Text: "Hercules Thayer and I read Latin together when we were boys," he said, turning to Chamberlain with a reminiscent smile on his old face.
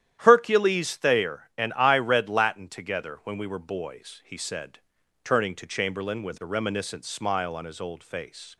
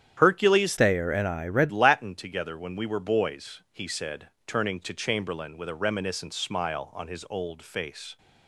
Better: first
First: starts louder than the rest; strong; until 1.2 s; 11 dB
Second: starts louder than the rest; strong; until 1.2 s; 10 dB // changes voice from "Thayer" to "read"; from 0.7 to 1.7 s; 1.0 s long

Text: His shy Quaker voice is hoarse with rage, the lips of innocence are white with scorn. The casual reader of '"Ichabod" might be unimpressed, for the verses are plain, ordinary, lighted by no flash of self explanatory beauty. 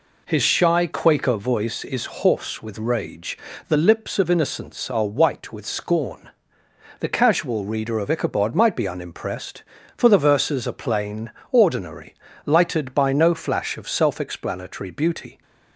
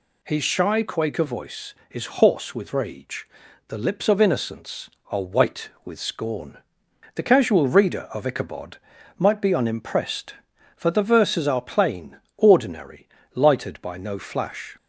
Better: first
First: none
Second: pauses between "Ichabod" and "might"; at 8.7 s; 0.42 s long // stops before "of self explanatory beauty"; at 14.7 s

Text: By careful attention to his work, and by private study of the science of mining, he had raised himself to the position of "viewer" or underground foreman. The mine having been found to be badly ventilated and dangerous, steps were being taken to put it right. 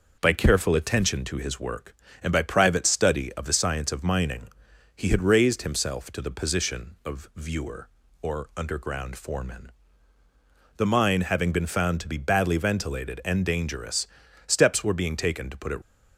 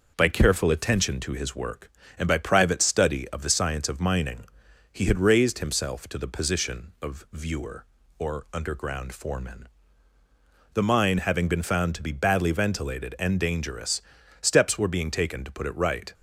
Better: second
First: stops before "right"; at 15.8 s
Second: none

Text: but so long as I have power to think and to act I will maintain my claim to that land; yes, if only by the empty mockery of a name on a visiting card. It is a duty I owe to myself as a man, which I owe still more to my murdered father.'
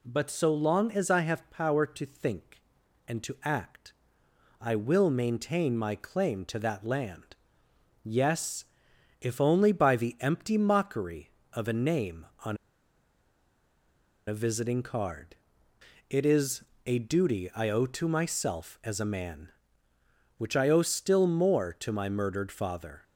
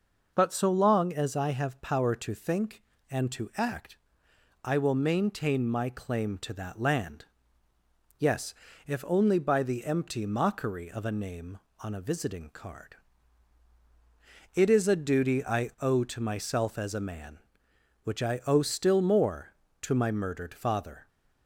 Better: second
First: pauses between "act" and "I"; noticeable; at 3.9 s; 0.70 s long // pauses between "on" and "a"; strong; at 12.5 s; 1.7 s long // pauses between "is" and "a"; slight; at 16.6 s; 0.22 s long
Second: pauses between "act" and "I"; noticeable; at 3.9 s; 0.70 s long

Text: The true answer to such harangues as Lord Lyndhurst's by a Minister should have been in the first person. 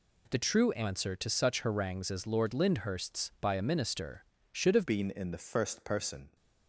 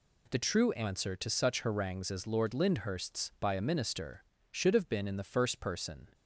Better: second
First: changes voice at "been"; from 4.8 s on; 1.5 s long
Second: none

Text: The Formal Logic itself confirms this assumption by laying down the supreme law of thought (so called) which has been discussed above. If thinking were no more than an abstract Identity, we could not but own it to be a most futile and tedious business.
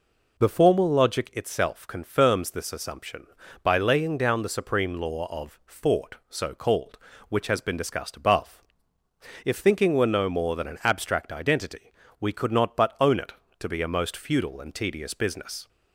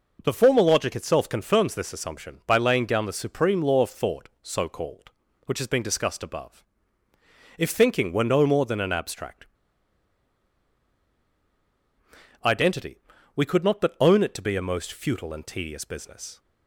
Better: first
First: none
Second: pauses between "abstract" and "Identity"; strong; at 9.4 s; 2.9 s long

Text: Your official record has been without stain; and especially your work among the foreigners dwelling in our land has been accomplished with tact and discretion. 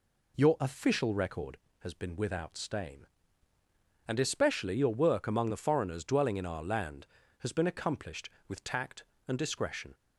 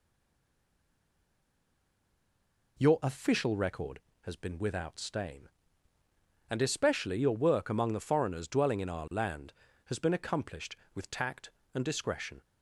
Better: first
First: none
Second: stays silent before the first word; strong; until 2.7 s; 2.7 s long

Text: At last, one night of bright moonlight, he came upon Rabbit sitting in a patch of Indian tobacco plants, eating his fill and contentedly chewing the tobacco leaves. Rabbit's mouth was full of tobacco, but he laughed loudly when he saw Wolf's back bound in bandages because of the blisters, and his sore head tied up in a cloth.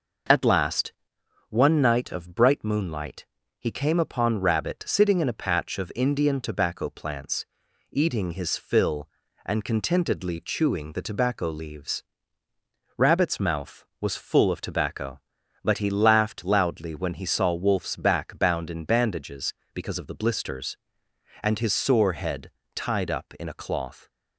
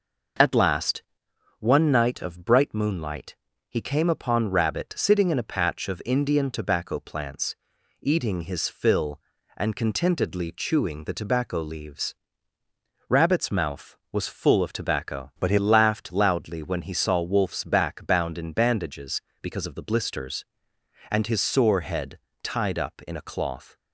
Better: first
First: pauses between "head" and "tied"; slight; at 22.4 s; 0.24 s long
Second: changes voice from "but" to "he"; from 15.3 to 15.5 s; 0.2 s long // pauses between "head" and "tied"; slight; at 22.1 s; 0.24 s long

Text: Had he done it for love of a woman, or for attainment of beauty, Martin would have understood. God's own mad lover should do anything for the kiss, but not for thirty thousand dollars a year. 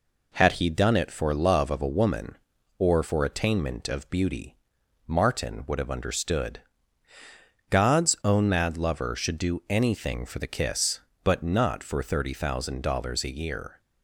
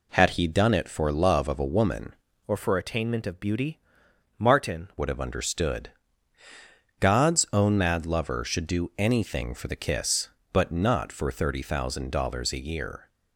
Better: first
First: none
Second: changes voice from "or" to "Martin"; from 2.4 to 4.8 s; 2.4 s long

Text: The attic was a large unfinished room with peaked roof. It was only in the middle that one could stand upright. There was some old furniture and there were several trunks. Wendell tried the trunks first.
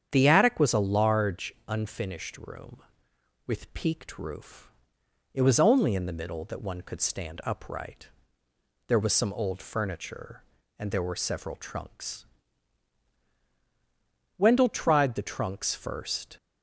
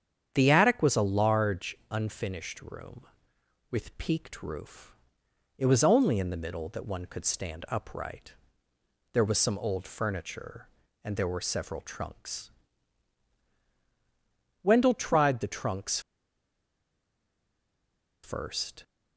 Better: first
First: starts louder than the rest; strong; until 1.1 s; 8.5 dB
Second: starts louder than the rest; strong; until 1.3 s; 8.5 dB // pauses between "trunks" and "first"; strong; at 15.9 s; 2.2 s long

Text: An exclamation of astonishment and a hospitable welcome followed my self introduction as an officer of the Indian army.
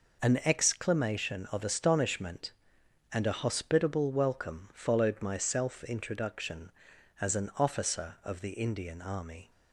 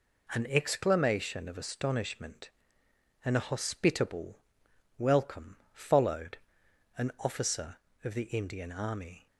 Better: first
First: none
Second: pauses between "hospitable" and "welcome"; noticeable; at 4.3 s; 0.60 s long // pauses between "welcome" and "followed"; slight; at 5.5 s; 0.16 s long // skips "my self introduction as"; at 6.6 s

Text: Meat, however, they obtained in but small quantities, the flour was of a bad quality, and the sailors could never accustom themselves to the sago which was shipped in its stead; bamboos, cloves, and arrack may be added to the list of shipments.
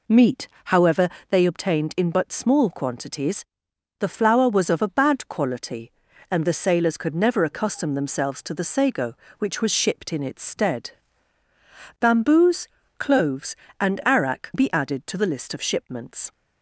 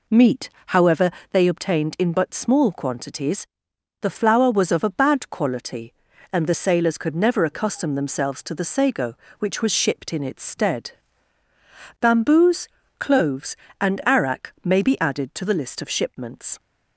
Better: second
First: skips "may"; at 14.5 s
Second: none

